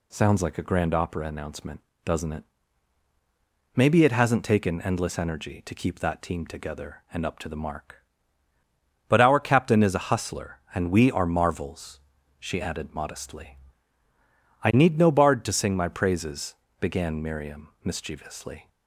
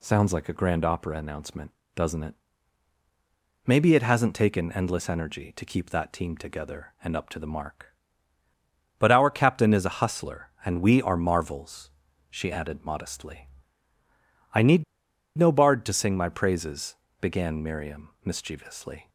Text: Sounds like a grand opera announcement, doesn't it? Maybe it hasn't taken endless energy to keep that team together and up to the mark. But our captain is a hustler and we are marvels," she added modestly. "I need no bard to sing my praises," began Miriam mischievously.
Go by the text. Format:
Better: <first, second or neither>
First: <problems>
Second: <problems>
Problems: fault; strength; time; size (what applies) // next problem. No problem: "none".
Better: first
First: none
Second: pauses between "need" and "no"; noticeable; at 14.8 s; 0.54 s long